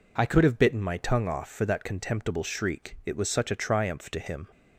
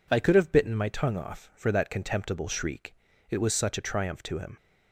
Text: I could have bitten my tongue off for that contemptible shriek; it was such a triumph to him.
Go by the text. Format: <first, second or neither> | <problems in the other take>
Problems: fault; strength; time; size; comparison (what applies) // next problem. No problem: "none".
neither | none